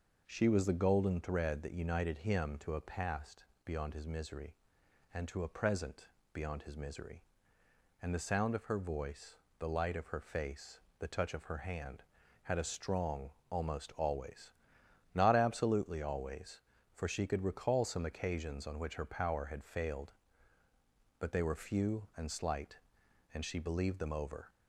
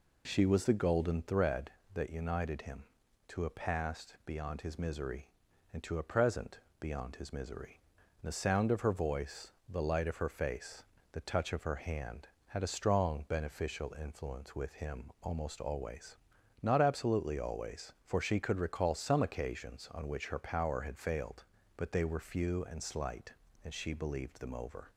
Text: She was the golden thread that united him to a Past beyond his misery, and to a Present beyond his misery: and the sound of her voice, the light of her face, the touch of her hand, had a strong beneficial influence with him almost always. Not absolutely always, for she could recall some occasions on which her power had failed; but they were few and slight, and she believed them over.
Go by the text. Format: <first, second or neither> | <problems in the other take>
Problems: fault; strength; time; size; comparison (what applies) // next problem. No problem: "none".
second | pauses between "Past" and "beyond"; slight; at 3.4 s; 0.18 s long // pauses between "Present" and "beyond"; slight; at 6.0 s; 0.24 s long; slight in the second // skips "beneficial influence with him"; at 13.4 s